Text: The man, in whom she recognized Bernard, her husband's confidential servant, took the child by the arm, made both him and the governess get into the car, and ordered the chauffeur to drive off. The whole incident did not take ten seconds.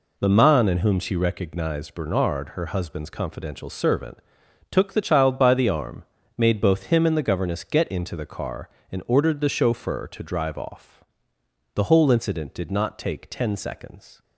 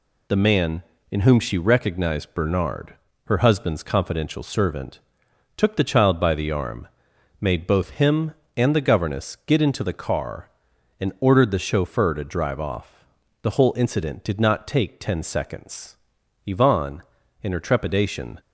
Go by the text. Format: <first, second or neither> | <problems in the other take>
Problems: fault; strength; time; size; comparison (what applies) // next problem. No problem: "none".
first | goes on to say "Yvonne in her trepidation"; strong; from 16.4 s on; 1.9 s long